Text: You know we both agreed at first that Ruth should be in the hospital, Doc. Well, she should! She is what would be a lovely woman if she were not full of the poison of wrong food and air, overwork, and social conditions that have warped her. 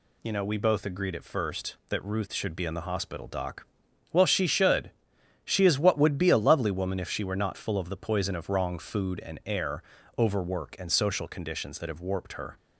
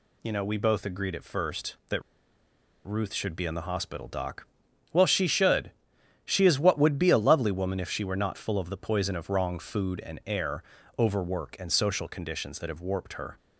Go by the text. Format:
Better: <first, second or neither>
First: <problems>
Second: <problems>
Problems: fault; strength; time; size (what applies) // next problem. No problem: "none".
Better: first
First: none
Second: pauses between "that" and "Ruth"; noticeable; at 2.0 s; 0.84 s long